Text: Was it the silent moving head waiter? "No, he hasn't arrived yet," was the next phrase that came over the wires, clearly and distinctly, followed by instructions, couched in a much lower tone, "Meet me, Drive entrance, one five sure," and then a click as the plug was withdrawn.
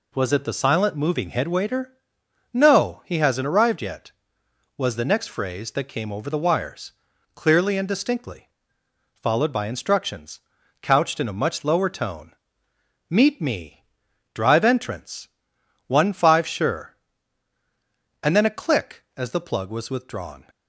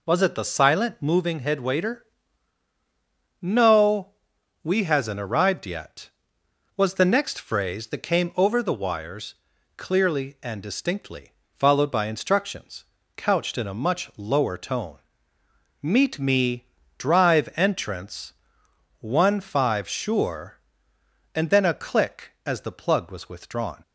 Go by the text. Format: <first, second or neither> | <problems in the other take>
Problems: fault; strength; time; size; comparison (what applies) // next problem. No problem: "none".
first | says "we" for "he"; at 4.6 s